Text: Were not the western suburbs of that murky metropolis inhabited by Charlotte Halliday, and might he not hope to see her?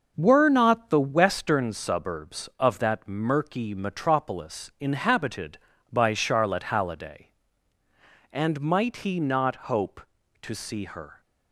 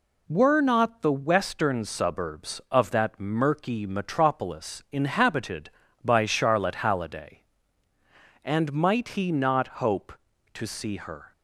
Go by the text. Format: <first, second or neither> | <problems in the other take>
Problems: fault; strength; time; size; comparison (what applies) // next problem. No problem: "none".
second | starts louder than the rest; noticeable; until 1.8 s; 6 dB